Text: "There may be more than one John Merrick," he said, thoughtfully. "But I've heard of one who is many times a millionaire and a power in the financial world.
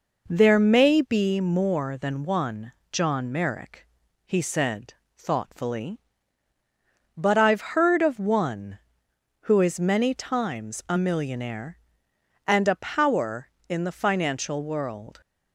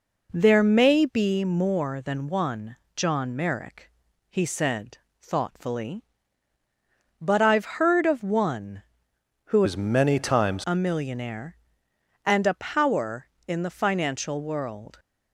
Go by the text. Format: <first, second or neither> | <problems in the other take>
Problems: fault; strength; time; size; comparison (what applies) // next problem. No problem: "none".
first | pauses between "one" and "John"; slight; at 2.7 s; 0.18 s long; slight in the first // changes voice from "is" to "times"; from 9.6 to 10.6 s; 1.0 s long